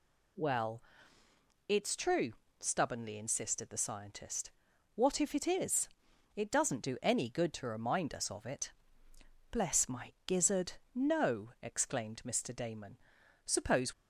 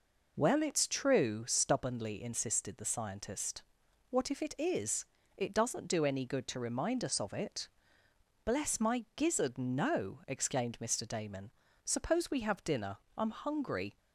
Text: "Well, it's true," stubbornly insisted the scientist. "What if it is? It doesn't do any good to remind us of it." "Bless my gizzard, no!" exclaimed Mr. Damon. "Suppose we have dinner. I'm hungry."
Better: second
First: stops before "we have dinner I'm hungry"; at 13.9 s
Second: none

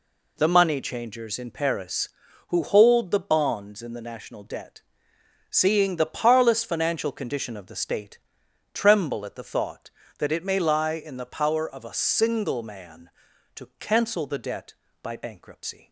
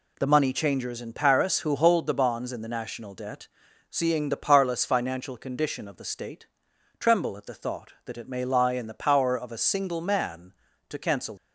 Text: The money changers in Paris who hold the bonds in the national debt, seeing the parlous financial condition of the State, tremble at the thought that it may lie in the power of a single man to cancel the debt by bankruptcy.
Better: first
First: none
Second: stops before "the debt by bankruptcy"; at 11.3 s

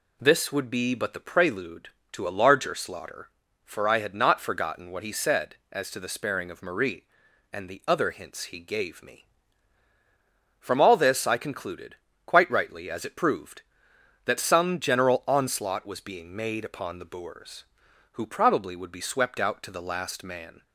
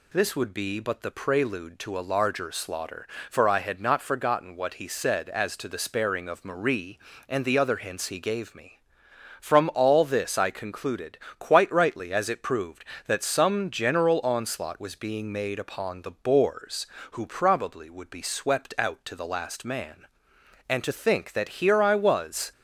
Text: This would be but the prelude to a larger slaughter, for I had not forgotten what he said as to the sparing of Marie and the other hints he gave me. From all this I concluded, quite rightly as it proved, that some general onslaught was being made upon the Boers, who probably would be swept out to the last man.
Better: first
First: none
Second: goes on to say "And to think that here I was"; strong; from 20.6 s on; 1.8 s long

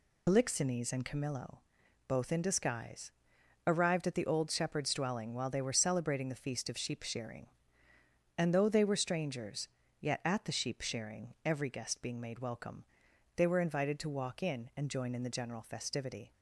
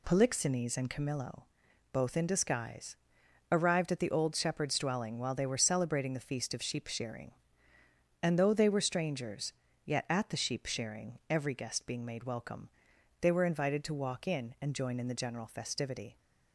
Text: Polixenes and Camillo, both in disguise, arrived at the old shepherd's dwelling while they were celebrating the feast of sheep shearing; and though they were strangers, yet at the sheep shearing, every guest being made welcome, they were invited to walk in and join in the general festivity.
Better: second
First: loses the start of "Polixenes"; at 0.2 s; 80 ms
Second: none

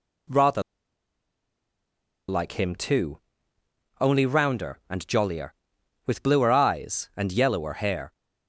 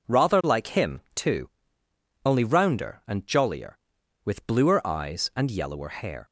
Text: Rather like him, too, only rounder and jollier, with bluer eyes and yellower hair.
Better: second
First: pauses between "Rather" and "like"; strong; at 0.6 s; 1.6 s long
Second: none

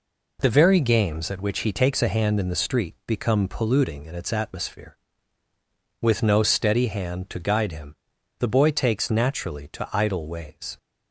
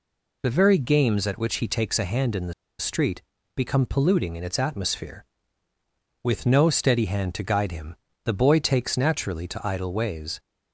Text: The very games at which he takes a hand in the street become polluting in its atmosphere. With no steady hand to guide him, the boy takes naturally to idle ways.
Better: first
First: none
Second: pauses between "the" and "street"; slight; at 2.5 s; 0.25 s long // pauses between "street" and "become"; slight; at 3.2 s; 0.34 s long

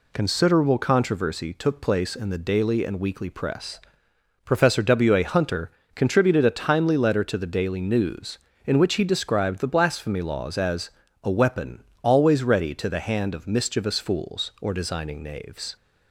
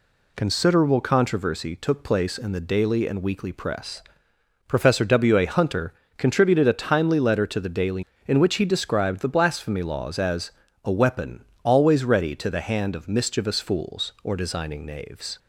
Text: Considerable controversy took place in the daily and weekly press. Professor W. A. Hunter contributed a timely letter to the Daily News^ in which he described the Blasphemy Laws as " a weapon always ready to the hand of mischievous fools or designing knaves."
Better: first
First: pauses between "Hunter" and "contributed"; slight; at 5.7 s; 0.24 s long // pauses between "weapon" and "always"; slight; at 11.8 s; 0.18 s long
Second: pauses between "Hunter" and "contributed"; slight; at 5.9 s; 0.24 s long // skips "News"; at 8.1 s // pauses between "weapon" and "always"; slight; at 11.4 s; 0.18 s long

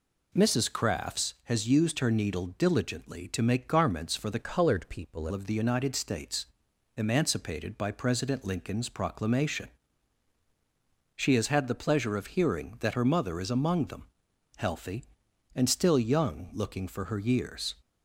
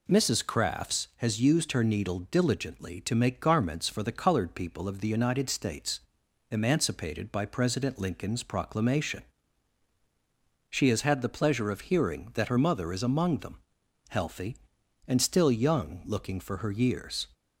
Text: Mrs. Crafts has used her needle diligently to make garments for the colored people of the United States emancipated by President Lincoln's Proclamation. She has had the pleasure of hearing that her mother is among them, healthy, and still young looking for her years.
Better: second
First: changes voice from "colored" to "people"; from 4.4 to 5.2 s; 0.8 s long // pauses between "States" and "emancipated"; noticeable; at 6.4 s; 0.50 s long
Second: pauses between "States" and "emancipated"; noticeable; at 6.0 s; 0.50 s long

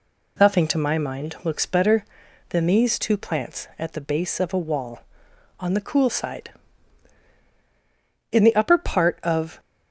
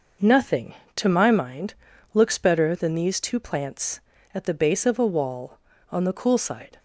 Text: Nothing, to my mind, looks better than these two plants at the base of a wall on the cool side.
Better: second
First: goes on to say "In the upper part of"; noticeable; from 8.3 s on; 1.2 s long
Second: none

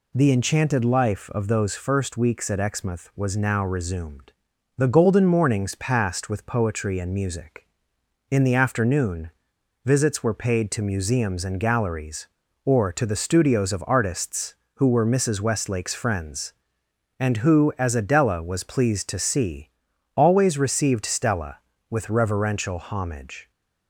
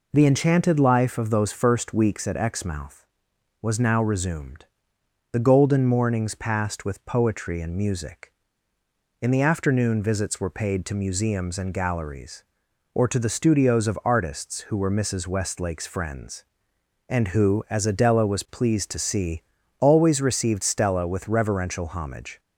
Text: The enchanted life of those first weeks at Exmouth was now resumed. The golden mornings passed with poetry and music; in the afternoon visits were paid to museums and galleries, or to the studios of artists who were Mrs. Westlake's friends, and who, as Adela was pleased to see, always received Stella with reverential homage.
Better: second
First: pauses between "afternoon" and "visits"; noticeable; at 9.3 s; 0.53 s long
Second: none

